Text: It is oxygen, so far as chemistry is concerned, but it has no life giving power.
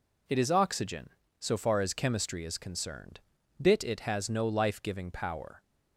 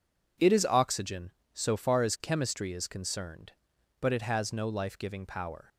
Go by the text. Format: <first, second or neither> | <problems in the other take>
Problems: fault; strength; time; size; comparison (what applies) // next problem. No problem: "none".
second | says "bit" for "but"; at 3.6 s